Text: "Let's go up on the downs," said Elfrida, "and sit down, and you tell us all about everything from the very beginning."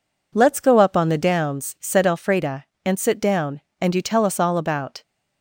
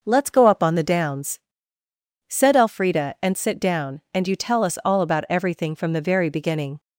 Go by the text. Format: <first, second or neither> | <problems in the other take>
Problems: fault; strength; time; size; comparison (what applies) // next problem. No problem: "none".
second | stops before "everything from the very beginning"; at 5.0 s